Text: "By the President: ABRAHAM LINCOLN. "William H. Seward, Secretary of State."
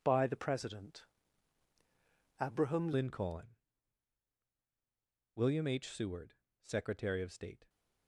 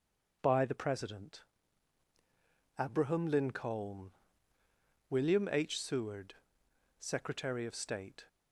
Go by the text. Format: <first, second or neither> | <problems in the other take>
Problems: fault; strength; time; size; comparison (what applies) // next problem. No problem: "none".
second | changes voice at "LINCOLN"; from 2.9 s on; 4.7 s long